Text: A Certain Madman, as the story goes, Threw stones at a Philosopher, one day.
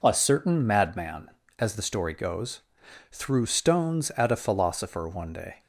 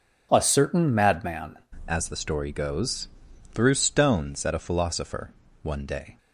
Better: first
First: none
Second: changes voice at "as"; from 1.8 s on; 4.3 s long

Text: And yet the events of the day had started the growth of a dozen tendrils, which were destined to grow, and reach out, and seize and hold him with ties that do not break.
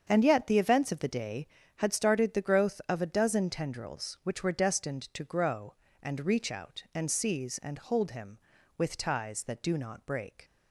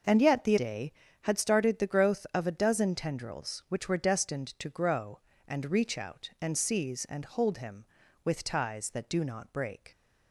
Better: first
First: starts louder than the rest; strong; until 1.0 s; 7.5 dB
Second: starts louder than the rest; noticeable; until 1.3 s; 6 dB // skips "events of the"; at 0.5 s

